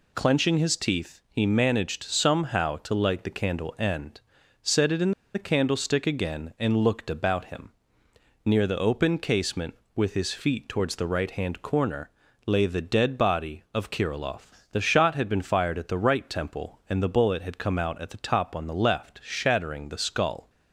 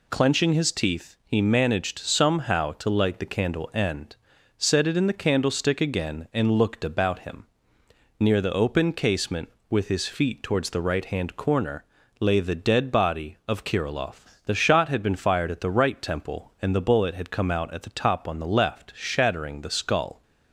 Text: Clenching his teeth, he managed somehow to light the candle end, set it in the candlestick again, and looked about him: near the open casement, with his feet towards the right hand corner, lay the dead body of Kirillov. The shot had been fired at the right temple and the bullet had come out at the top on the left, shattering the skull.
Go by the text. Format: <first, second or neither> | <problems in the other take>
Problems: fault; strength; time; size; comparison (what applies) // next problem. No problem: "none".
second | pauses between "in" and "the"; slight; at 5.1 s; 0.22 s long